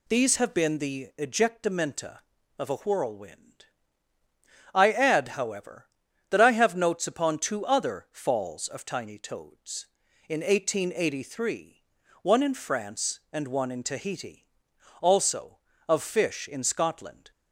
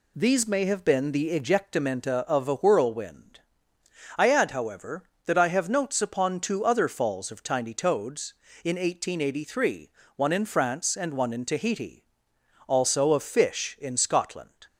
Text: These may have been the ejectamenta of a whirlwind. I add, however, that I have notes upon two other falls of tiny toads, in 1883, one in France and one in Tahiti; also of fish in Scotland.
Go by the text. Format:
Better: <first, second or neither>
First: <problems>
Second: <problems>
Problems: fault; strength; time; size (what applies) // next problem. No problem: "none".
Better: second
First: skips "may"; at 0.3 s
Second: none